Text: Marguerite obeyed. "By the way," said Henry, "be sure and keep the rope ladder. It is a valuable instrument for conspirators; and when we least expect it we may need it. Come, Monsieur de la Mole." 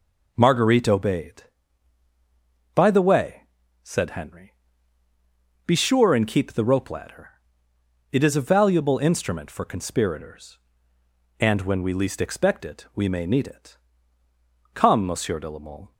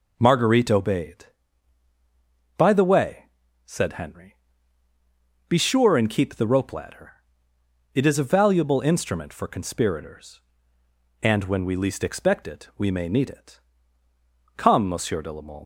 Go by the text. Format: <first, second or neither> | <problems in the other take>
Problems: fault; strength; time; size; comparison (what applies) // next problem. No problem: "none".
first | leaves "Mole" unfinished; at 15.6 s; 105 ms